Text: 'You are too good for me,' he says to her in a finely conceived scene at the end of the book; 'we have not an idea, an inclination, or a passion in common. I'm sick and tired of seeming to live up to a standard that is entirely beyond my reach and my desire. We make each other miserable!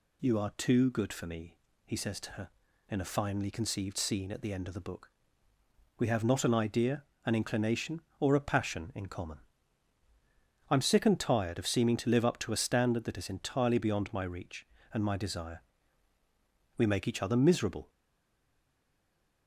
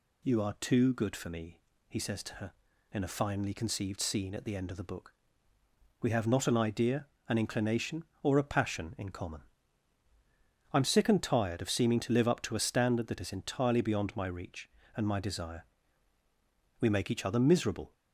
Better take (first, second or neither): second